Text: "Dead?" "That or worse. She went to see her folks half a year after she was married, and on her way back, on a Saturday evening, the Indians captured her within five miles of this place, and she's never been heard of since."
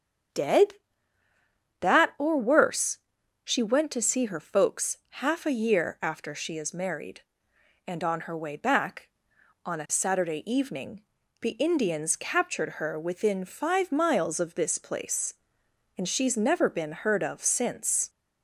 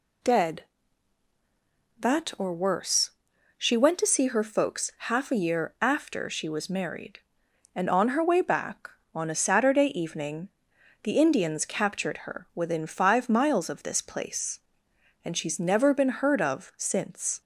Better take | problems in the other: second | starts louder than the rest; until 2.4 s; 7 dB // pauses between "folks" and "half"; slight; at 4.9 s; 0.26 s long; slight in the second // says "is" for "was"; at 6.5 s

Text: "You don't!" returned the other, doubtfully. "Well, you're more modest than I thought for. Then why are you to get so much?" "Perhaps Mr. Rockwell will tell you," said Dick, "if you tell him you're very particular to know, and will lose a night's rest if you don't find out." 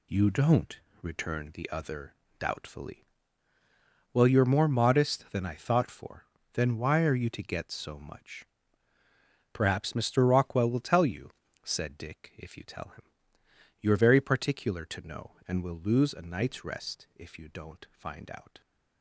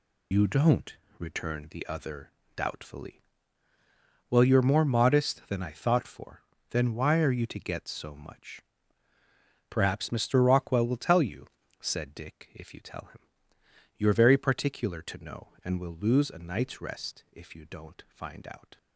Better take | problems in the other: first | loses the start of "You"; at 0.3 s; 40 ms // pauses between "him" and "you're"; noticeable; at 13.1 s; 0.78 s long; noticeable in the first

